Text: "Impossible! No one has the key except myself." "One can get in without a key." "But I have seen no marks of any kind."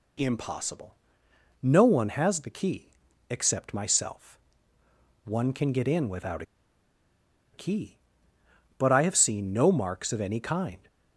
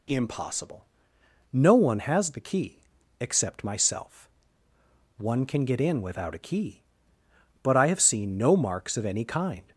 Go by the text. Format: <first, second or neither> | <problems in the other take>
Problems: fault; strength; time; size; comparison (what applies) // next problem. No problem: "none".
second | pauses between "key" and "except"; at 2.9 s; 0.38 s long; also in the second // pauses between "without" and "a"; at 6.4 s; 1.1 s long